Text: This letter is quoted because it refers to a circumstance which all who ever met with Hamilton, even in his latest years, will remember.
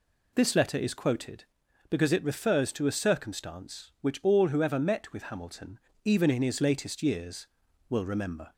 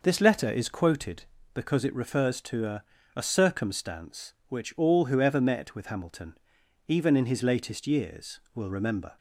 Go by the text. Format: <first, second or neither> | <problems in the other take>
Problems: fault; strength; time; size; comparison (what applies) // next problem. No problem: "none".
first | says "a" twice; at 3.1 s